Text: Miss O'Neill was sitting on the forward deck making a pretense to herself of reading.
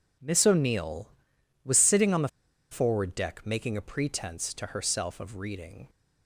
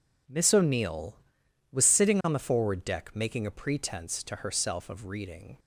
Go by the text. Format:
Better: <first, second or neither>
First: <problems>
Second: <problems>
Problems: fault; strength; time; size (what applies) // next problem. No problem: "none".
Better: second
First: pauses between "the" and "forward"; at 2.2 s; 0.43 s long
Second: none